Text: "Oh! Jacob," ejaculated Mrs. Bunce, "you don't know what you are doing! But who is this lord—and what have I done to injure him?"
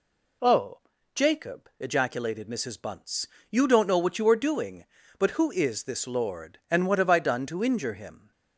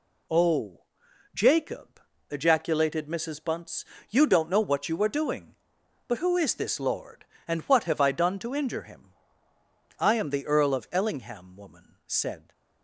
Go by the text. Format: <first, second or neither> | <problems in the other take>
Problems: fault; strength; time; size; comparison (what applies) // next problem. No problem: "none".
first | goes on to say "I am the Earl of Ellingham woman said"; strong; from 9.9 s on; 2.5 s long